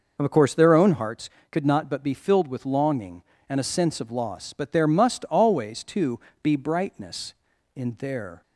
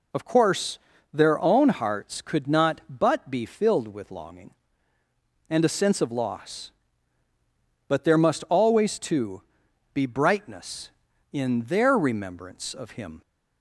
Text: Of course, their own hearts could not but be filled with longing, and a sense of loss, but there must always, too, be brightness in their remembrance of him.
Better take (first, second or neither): second